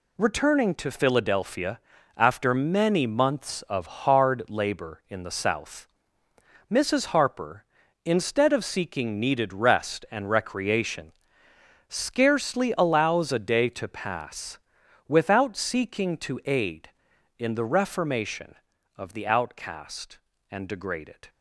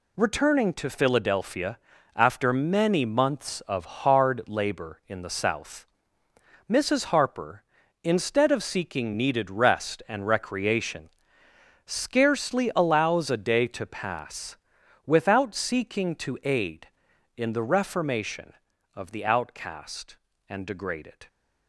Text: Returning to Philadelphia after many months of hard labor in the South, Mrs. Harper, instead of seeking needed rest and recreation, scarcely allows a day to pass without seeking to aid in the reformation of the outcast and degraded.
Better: neither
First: pauses between "Philadelphia" and "after"; at 1.8 s; 0.38 s long // pauses between "pass" and "without"; noticeable; at 14.5 s; 0.50 s long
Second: pauses between "Philadelphia" and "after"; at 1.7 s; 0.38 s long // pauses between "pass" and "without"; noticeable; at 14.5 s; 0.50 s long

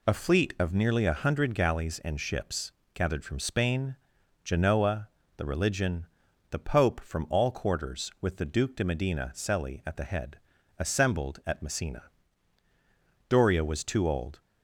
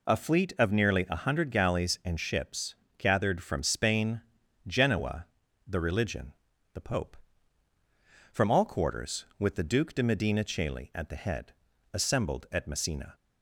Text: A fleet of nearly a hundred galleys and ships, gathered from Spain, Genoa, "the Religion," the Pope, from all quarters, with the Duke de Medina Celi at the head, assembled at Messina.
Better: second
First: goes on to say "Doria was too old"; noticeable; from 13.2 s on; 1.2 s long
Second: none

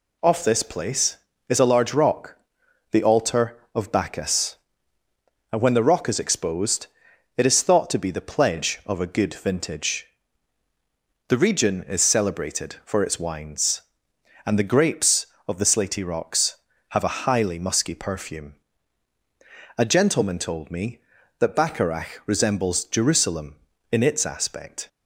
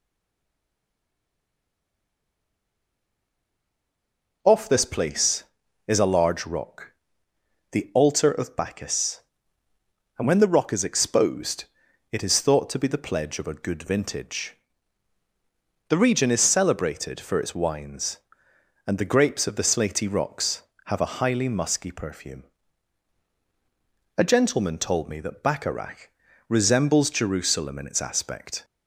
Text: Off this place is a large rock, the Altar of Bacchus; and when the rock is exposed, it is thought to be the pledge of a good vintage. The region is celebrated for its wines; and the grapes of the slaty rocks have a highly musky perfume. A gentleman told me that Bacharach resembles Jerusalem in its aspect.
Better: first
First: none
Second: stays silent before the first word; strong; until 4.4 s; 4.4 s long // pauses between "Bacharach" and "resembles"; at 26.0 s; 0.40 s long

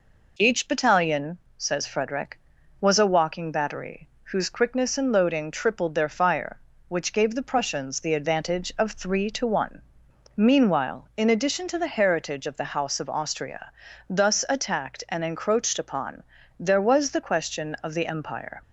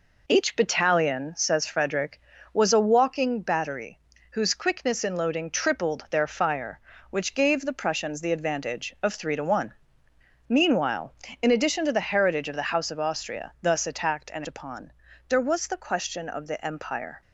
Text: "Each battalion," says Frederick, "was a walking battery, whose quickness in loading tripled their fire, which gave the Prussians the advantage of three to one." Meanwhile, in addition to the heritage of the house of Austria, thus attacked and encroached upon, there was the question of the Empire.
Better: first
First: none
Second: skips "encroached"; at 14.4 s

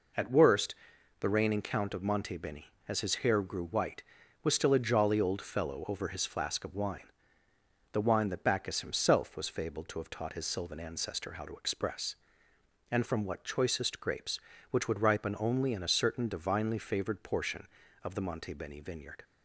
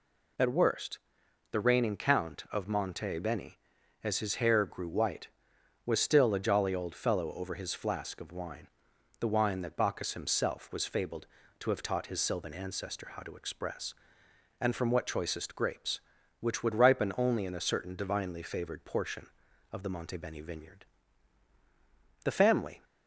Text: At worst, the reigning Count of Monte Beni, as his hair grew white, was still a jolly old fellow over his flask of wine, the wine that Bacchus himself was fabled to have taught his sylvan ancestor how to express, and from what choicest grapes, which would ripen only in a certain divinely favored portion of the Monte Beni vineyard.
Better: first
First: none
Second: goes on to say "The family"; from 22.2 s on; 0.60 s long

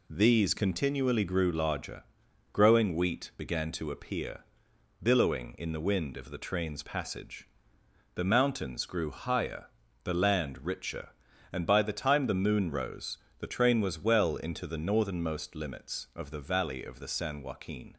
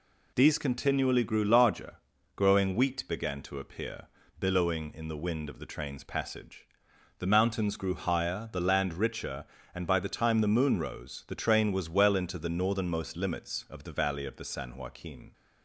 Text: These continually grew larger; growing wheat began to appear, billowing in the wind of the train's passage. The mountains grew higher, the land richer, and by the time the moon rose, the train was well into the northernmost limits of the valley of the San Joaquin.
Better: neither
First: none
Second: none

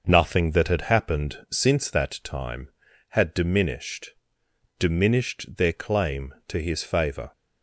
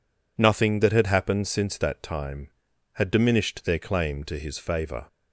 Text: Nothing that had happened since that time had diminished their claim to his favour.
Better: second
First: starts louder than the rest; noticeable; until 1.0 s; 6 dB // says "diminished" twice; at 4.7 s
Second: none

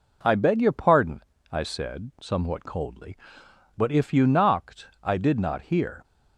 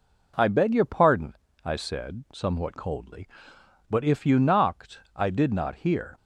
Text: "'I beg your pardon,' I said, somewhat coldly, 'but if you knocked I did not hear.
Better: neither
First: none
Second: none

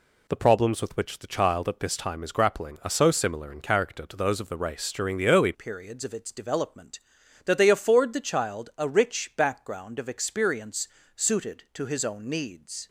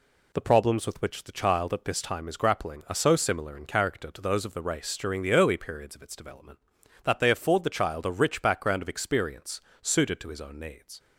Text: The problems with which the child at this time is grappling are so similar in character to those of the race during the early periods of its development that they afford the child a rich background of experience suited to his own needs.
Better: second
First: changes voice at "periods"; from 5.5 s on; 7.3 s long // pauses between "experience" and "suited"; slight; at 10.8 s; 0.30 s long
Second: pauses between "experience" and "suited"; slight; at 9.5 s; 0.24 s long

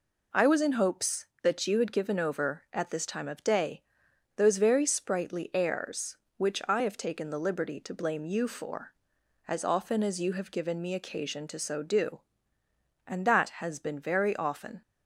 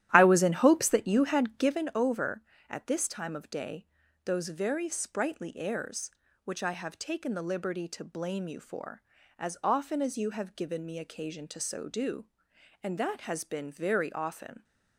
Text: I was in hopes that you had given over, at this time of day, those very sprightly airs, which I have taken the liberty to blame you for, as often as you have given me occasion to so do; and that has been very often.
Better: first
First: none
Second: starts louder than the rest; strong; until 1.9 s; 13 dB

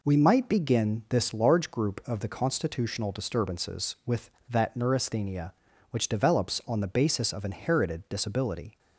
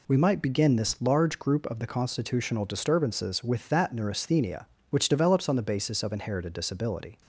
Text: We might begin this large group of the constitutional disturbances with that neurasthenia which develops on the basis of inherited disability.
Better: neither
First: none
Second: none

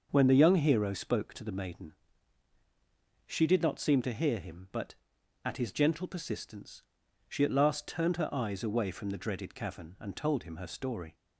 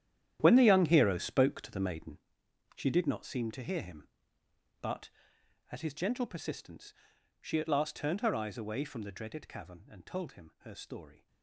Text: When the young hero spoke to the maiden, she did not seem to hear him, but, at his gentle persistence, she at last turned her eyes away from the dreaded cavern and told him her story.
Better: first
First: starts louder than the rest; noticeable; until 1.1 s; 6 dB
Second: gets quieter; strong; throughout; 14 dB // starts louder than the rest; strong; until 1.4 s; 10.5 dB

